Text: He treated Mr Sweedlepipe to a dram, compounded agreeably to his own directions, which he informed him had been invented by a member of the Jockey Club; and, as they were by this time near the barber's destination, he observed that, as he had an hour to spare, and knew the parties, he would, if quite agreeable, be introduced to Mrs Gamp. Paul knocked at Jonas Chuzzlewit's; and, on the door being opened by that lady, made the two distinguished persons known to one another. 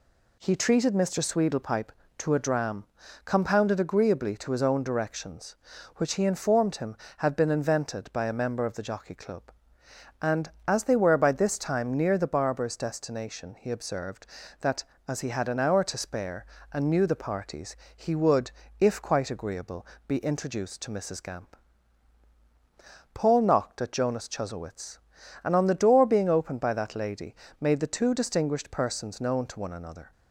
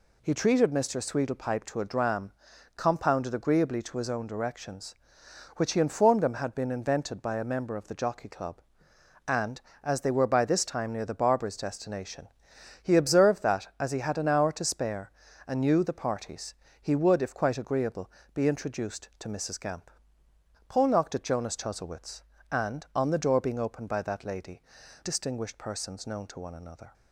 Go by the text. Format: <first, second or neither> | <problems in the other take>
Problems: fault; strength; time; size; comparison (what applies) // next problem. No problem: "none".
first | skips "made the two"; at 24.8 s